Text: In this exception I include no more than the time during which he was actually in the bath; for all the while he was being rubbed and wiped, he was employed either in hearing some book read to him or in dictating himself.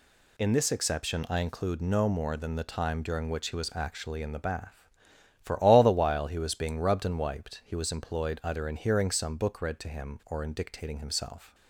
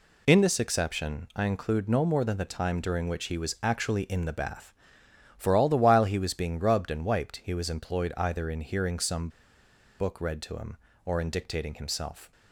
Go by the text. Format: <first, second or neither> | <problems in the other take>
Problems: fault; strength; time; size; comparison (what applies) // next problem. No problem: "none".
first | pauses between "some" and "book"; noticeable; at 9.2 s; 0.70 s long